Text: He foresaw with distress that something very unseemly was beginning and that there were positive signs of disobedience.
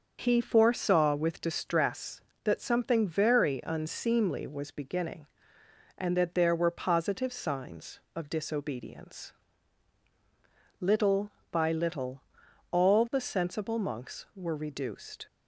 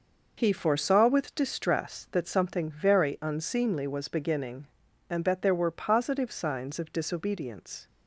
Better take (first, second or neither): second